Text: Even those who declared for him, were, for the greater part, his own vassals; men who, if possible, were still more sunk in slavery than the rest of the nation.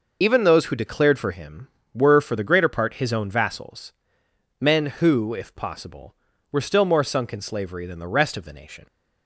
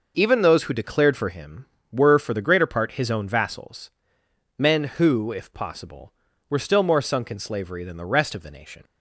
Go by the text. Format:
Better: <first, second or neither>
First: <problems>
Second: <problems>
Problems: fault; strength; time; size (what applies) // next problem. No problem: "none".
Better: second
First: loses the start of "Even"; at 0.2 s; 30 ms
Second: none